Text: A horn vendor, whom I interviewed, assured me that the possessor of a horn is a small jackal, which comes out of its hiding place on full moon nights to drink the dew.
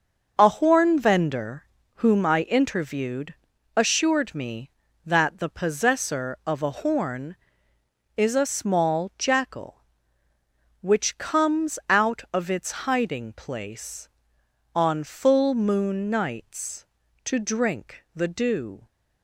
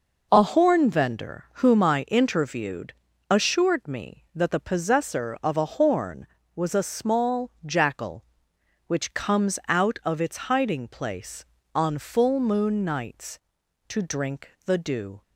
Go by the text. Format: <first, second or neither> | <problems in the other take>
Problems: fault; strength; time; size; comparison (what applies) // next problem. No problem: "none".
first | says "was" for "is"; at 6.5 s // pauses between "drink" and "the"; slight; at 14.4 s; 0.16 s long